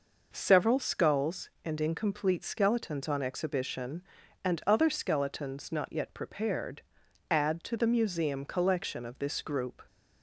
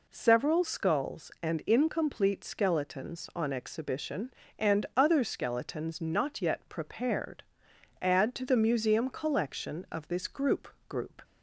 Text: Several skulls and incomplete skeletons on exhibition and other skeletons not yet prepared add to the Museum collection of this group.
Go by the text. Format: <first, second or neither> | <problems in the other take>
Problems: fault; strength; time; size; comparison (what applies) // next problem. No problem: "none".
first | pauses between "prepared" and "add"; noticeable; at 7.4 s; 0.58 s long; noticeable in the first // says "group" twice; at 10.8 s